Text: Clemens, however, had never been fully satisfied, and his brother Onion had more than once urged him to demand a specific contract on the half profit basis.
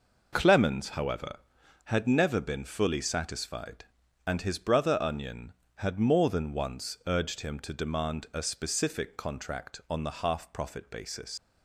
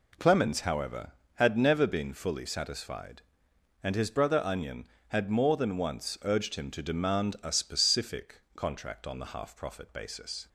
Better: second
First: leaves "basis" unfinished; at 11.3 s; 100 ms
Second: none

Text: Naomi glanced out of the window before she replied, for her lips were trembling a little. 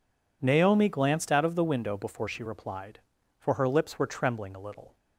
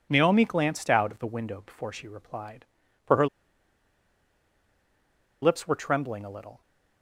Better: first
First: none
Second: pauses between "her" and "lips"; strong; at 3.2 s; 2.1 s long

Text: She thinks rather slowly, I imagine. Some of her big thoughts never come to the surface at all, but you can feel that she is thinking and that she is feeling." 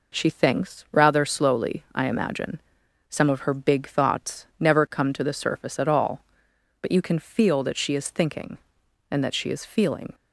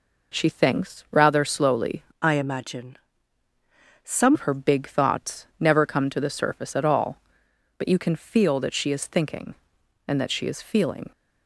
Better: first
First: none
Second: changes voice from "I" to "Some"; from 2.1 to 4.3 s; 2.2 s long

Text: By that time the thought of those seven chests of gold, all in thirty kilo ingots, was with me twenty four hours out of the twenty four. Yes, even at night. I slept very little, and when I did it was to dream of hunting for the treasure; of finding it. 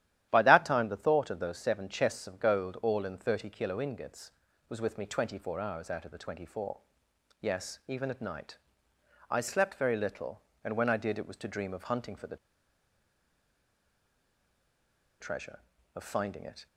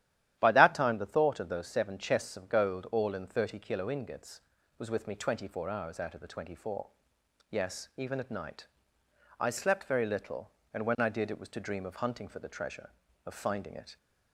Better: second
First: starts louder than the rest; strong; until 1.3 s; 12 dB // pauses between "the" and "treasure"; strong; at 12.3 s; 2.8 s long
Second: starts louder than the rest; strong; until 1.4 s; 12 dB

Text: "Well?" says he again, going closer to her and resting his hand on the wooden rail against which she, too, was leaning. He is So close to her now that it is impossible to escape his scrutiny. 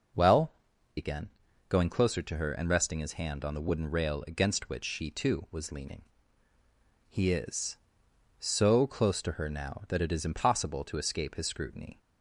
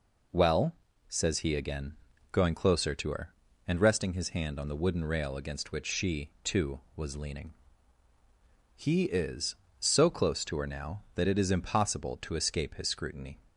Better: second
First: skips "says he"; at 0.7 s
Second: none

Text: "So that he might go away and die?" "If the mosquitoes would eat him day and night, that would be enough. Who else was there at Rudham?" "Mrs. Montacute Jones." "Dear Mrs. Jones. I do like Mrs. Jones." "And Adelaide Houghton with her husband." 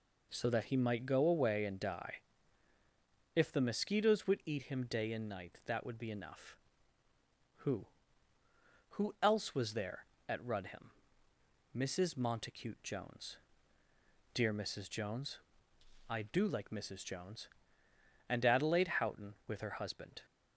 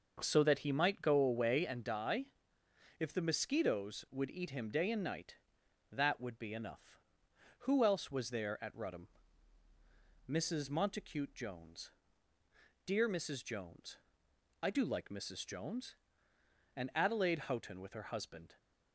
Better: second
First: says "Who" twice; at 8.9 s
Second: none

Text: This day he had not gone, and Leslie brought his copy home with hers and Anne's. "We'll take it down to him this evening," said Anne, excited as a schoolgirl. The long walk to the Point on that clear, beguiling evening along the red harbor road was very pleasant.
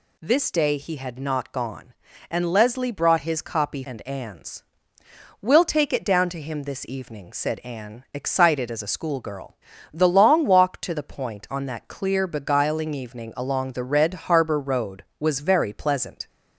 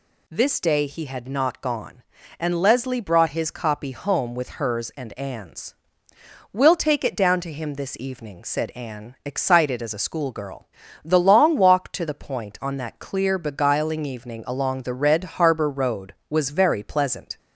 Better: second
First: skips "home with hers"; at 3.8 s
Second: none

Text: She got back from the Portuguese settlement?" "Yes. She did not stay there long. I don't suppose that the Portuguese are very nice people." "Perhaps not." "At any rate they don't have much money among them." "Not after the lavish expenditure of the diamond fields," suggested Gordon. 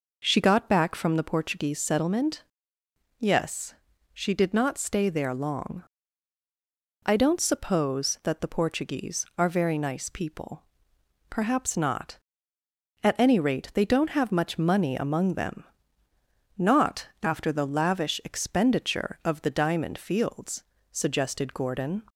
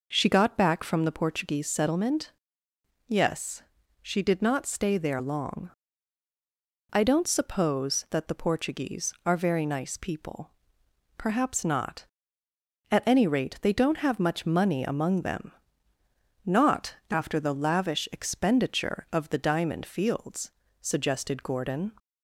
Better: neither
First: none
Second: none

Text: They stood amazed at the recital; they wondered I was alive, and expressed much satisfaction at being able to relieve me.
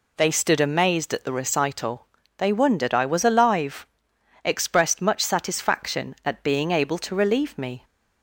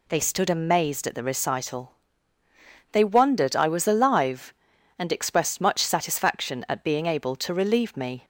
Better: second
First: skips "and"; at 4.1 s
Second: none

